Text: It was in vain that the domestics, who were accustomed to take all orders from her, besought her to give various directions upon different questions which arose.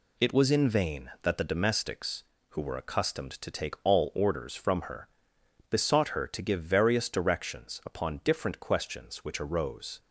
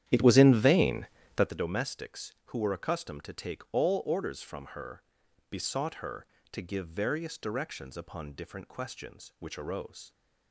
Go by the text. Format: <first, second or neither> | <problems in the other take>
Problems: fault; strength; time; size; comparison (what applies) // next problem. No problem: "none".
first | starts louder than the rest; strong; until 1.6 s; 10.5 dB